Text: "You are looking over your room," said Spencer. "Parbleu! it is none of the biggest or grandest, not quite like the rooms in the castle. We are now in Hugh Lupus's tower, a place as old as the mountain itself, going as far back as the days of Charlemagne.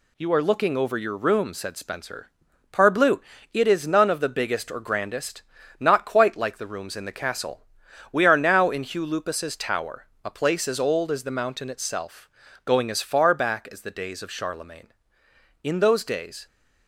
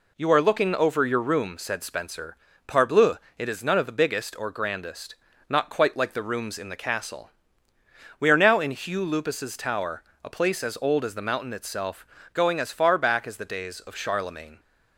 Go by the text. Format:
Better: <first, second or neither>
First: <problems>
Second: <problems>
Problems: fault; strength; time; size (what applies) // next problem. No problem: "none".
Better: second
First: goes on to say "In those days"; noticeable; from 15.6 s on; 0.82 s long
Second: none